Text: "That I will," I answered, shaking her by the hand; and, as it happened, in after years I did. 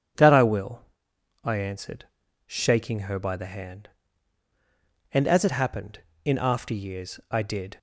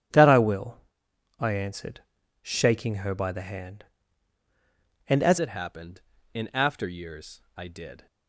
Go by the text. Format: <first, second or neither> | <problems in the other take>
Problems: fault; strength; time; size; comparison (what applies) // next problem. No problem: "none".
first | starts louder than the rest; strong; until 1.7 s; 11 dB // changes voice at "it"; from 5.3 s on; 2.7 s long // pauses between "years" and "I"; slight; at 7.4 s; 0.16 s long